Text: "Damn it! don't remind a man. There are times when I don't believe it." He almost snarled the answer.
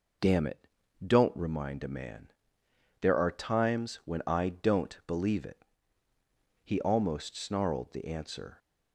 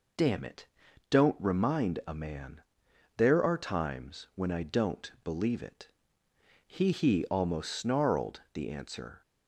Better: first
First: none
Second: says "He" twice; at 6.9 s

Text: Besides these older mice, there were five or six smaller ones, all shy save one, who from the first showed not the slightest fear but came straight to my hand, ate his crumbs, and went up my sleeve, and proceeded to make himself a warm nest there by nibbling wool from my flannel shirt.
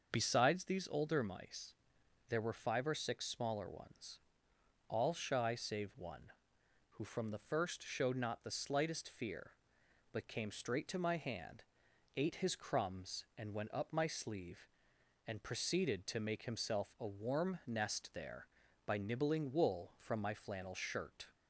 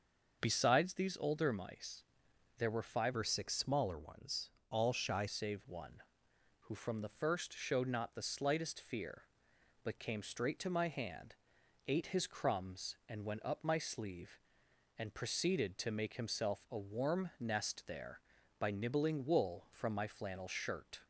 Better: first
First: starts louder than the rest; until 1.1 s; 6 dB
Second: starts louder than the rest; until 1.4 s; 6.5 dB // changes voice from "or" to "shy"; from 3.1 to 5.2 s; 2.1 s long

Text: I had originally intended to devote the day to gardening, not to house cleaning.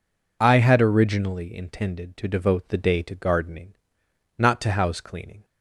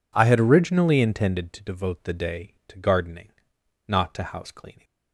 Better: neither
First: none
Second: none

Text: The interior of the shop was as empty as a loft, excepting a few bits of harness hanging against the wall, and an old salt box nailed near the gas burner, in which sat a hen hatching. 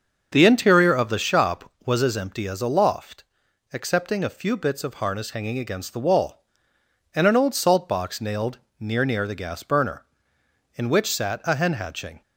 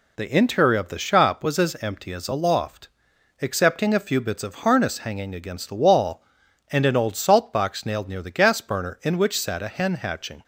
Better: second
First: starts louder than the rest; until 1.3 s; 6.5 dB // pauses between "nailed" and "near"; slight; at 8.5 s; 0.22 s long // says "near" twice; at 9.0 s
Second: none

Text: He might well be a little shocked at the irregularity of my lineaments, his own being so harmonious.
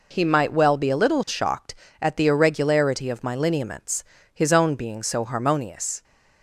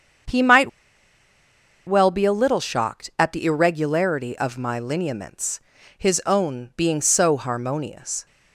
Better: first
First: none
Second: starts louder than the rest; strong; until 2.4 s; 7.5 dB // pauses between "might" and "well"; at 0.6 s; 1.1 s long

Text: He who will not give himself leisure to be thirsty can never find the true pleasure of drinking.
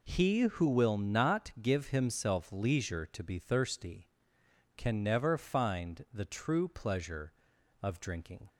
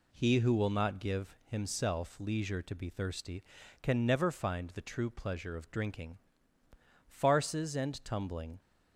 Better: first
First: none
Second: goes on to say "Farces and tumbling"; from 7.0 s on; 1.5 s long

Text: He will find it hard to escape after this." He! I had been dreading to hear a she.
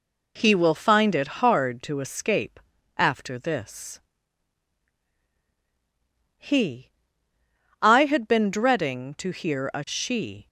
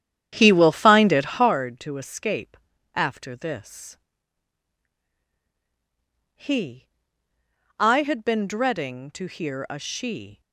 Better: first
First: pauses between "escape" and "after"; at 2.6 s; 0.38 s long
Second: starts louder than the rest; strong; until 1.6 s; 10 dB // pauses between "escape" and "after"; at 2.5 s; 0.38 s long

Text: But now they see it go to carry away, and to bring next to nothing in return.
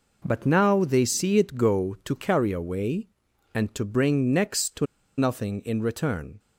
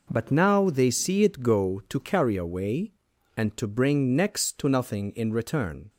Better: second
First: pauses between "to" and "nothing"; slight; at 4.8 s; 0.32 s long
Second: none

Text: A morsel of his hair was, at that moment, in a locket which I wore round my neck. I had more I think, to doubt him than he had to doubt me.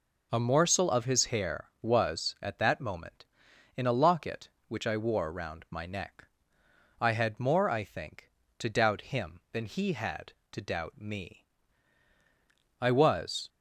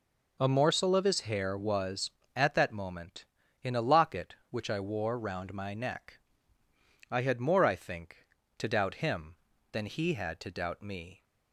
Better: second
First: goes on to say "I was"; noticeable; from 12.7 s on; 0.70 s long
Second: none

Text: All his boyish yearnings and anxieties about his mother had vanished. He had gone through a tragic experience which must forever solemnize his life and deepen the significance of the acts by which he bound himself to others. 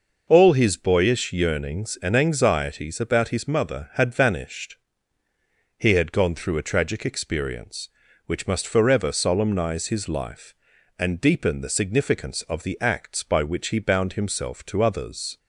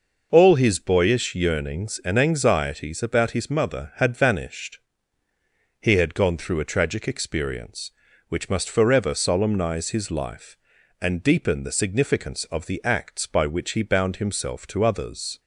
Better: neither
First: none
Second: none

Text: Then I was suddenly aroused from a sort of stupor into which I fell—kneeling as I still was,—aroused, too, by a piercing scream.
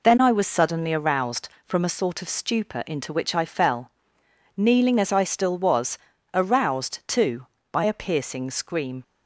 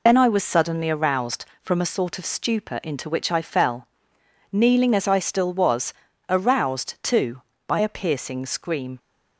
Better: first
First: none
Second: loses the start of "Then"; at 0.0 s; 45 ms

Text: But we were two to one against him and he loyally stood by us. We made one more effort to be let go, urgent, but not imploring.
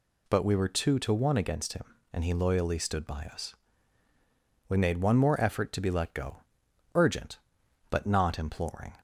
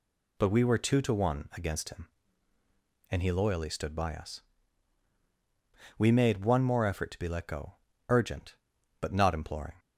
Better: neither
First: none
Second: none

